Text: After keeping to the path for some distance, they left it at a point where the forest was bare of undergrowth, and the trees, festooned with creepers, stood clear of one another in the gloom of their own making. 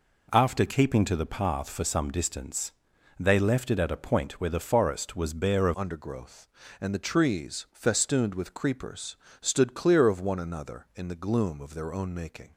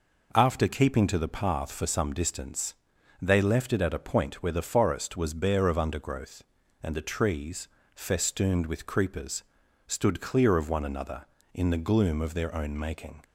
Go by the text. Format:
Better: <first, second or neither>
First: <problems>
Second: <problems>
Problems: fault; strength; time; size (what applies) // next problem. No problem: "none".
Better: second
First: changes voice at "undergrowth"; from 5.7 s on; 6.8 s long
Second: none